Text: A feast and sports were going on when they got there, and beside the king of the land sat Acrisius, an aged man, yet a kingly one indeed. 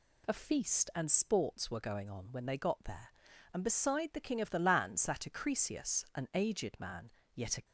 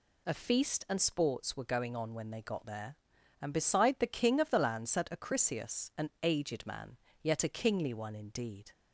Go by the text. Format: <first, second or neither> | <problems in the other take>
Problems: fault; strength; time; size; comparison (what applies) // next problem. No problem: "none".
second | stops before "kingly one indeed"; at 7.6 s